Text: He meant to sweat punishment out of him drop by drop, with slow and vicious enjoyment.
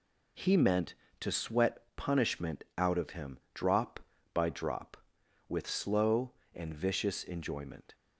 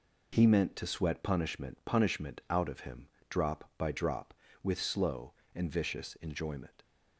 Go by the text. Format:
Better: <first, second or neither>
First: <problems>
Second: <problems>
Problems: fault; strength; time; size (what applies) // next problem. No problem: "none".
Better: first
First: pauses between "him" and "drop"; slight; at 3.3 s; 0.16 s long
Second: says "punishment" twice; at 1.8 s // pauses between "him" and "drop"; slight; at 3.0 s; 0.24 s long